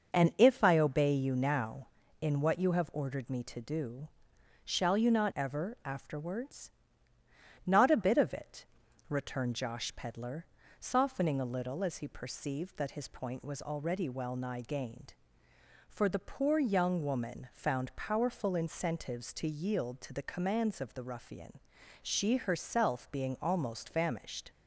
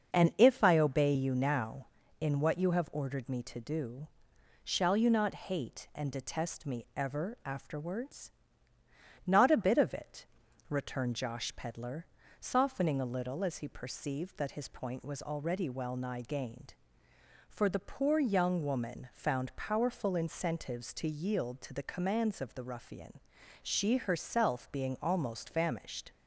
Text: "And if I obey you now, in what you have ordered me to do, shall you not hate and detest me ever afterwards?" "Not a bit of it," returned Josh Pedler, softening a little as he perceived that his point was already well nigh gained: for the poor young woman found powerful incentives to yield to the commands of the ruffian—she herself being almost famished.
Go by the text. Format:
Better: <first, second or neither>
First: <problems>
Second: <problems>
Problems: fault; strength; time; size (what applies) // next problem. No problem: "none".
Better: second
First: starts louder than the rest; until 1.1 s; 6.5 dB // skips "hate and detest me"; at 5.3 s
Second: starts louder than the rest; until 1.1 s; 6.5 dB